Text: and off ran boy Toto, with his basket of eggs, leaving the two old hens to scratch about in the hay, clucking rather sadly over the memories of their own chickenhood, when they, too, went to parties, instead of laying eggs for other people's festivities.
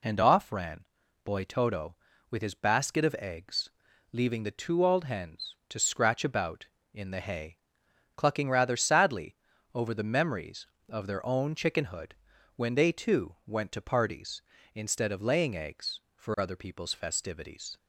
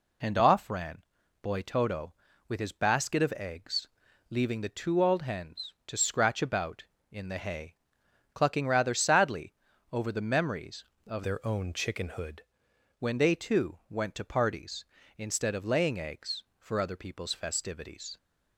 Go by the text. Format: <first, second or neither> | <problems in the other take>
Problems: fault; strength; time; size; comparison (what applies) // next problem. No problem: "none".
first | pauses between "ran" and "boy"; at 0.9 s; 0.42 s long; also in the first // pauses between "sadly" and "over"; at 9.5 s; 0.38 s long; also in the first // changes voice from "their" to "chickenhood"; from 11.2 to 12.3 s; 1.1 s long